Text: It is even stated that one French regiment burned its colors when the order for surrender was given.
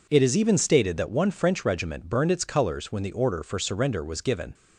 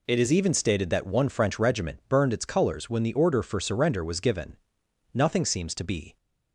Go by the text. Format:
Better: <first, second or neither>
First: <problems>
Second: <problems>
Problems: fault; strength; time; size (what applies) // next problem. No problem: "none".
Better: first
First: none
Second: goes on to say "Nothing seems to be"; noticeable; from 5.1 s on; 1.0 s long